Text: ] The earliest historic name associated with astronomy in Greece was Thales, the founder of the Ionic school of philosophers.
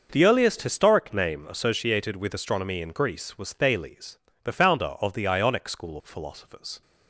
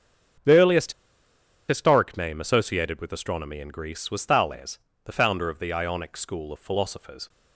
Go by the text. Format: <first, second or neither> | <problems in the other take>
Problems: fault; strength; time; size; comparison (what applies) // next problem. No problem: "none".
first | starts louder than the rest; until 2.2 s; 7 dB // pauses between "earliest" and "historic"; noticeable; at 0.9 s; 0.75 s long